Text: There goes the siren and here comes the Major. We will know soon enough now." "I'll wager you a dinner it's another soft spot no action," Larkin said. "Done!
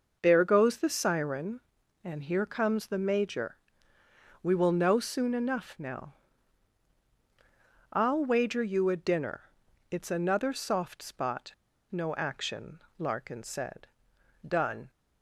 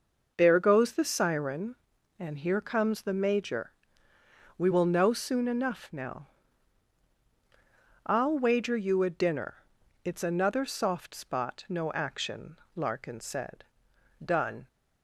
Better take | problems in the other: second | pauses between "dinner" and "it's"; noticeable; at 9.4 s; 0.48 s long; noticeable in the second // pauses between "spot" and "no"; at 11.5 s; 0.37 s long

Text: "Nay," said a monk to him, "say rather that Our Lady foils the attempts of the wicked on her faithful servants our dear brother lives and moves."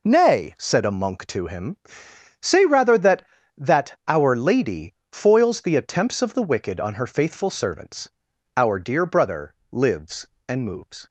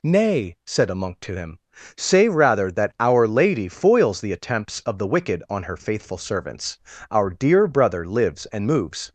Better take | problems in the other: second | says "that" twice; at 3.5 s // pauses between "Lady" and "foils"; slight; at 4.9 s; 0.22 s long // pauses between "servants" and "our"; noticeable; at 8.0 s; 0.48 s long; slight in the second // pauses between "brother" and "lives"; slight; at 9.5 s; 0.18 s long

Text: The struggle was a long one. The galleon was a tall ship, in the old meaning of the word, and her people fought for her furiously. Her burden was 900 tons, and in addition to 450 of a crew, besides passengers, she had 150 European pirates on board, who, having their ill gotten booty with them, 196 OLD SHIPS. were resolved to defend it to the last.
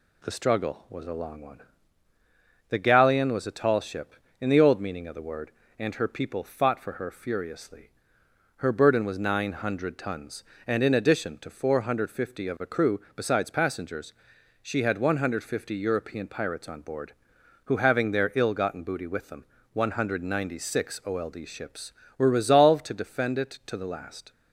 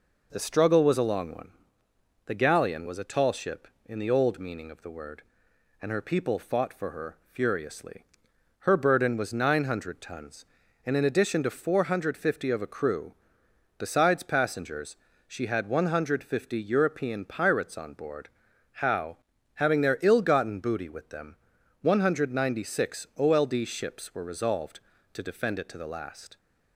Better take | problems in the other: first | pauses between "her" and "furiously"; slight; at 7.1 s; 0.16 s long // says "how" for "who"; at 18.7 s

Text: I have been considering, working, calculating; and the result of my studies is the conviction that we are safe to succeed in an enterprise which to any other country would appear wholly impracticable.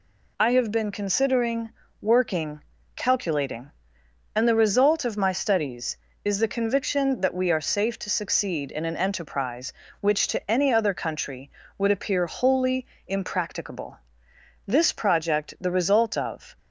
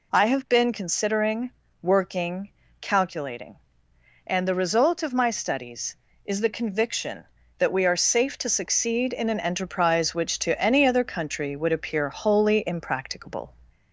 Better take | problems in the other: second | pauses between "wholly" and "impracticable"; slight; at 12.8 s; 0.22 s long // goes on to say "This project the result of"; strong; from 14.6 s on; 1.9 s long

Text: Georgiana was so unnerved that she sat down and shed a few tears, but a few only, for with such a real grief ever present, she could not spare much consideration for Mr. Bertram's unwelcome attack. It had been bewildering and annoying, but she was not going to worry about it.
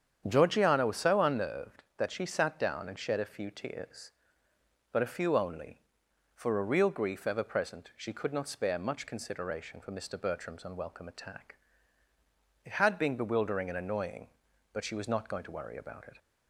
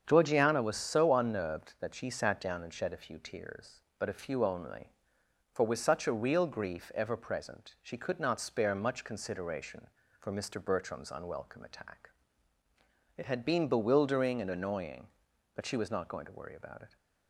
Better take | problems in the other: second | starts louder than the rest; strong; until 1.2 s; 8.5 dB; strong in the second // skips "with such"; at 6.6 s

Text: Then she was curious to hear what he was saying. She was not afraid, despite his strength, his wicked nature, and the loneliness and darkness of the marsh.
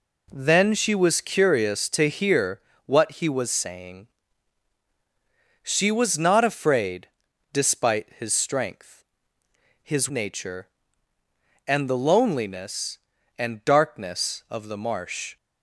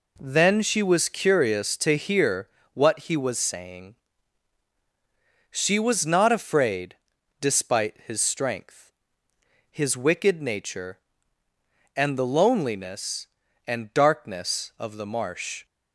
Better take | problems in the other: second | pauses between "hear" and "what"; slight; at 2.6 s; 0.24 s long; slight in the second // skips "wicked"; at 10.0 s

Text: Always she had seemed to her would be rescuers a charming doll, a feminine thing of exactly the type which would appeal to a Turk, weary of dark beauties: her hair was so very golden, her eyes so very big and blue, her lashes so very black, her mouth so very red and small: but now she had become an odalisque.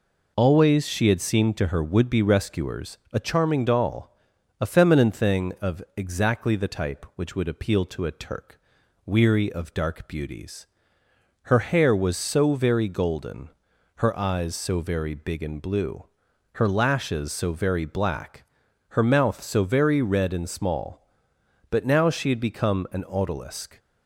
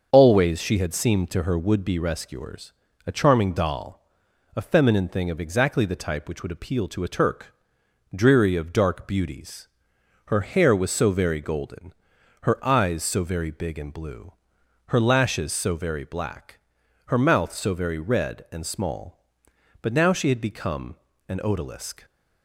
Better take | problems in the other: first | starts louder than the rest; until 1.1 s; 6.5 dB // pauses between "rescuers" and "a"; slight; at 2.7 s; 0.36 s long // says "dreary" for "weary"; at 8.1 s // pauses between "become" and "an"; slight; at 20.9 s; 0.32 s long

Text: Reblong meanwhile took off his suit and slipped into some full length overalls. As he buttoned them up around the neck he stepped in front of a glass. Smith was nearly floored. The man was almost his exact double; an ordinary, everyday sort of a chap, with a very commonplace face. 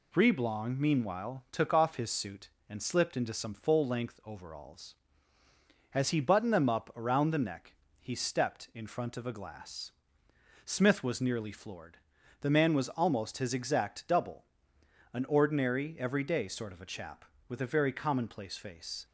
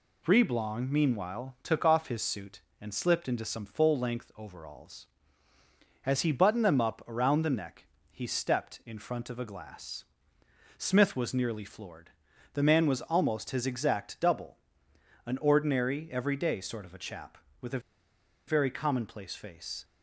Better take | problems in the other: first | pauses between "neck" and "he"; slight; at 7.8 s; 0.26 s long; slight in the first // pauses between "a" and "very"; noticeable; at 17.8 s; 0.67 s long

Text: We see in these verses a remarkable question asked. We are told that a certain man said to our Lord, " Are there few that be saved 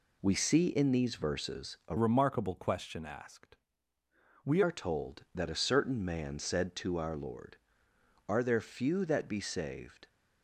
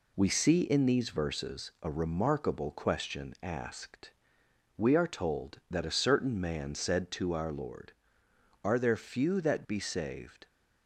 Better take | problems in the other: second | changes voice from "remarkable" to "We"; from 1.9 to 4.6 s; 2.7 s long

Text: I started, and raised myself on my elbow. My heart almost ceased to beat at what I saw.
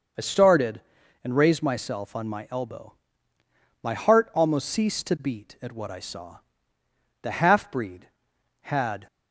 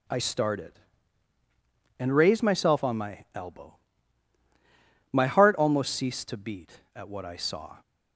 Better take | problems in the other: second | goes on to say "The half breed had"; strong; from 7.2 s on; 1.8 s long

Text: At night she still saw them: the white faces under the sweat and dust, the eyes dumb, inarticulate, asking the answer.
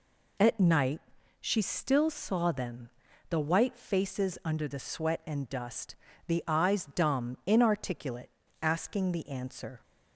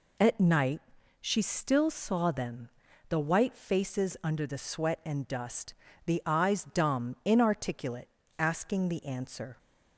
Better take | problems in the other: neither | pauses between "night" and "she"; the same in both

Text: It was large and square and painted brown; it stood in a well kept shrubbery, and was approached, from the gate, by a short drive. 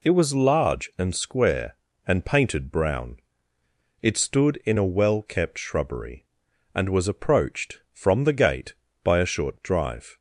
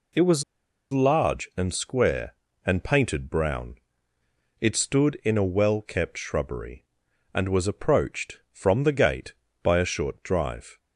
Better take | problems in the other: first | pauses between "was" and "large"; noticeable; at 0.4 s; 0.50 s long

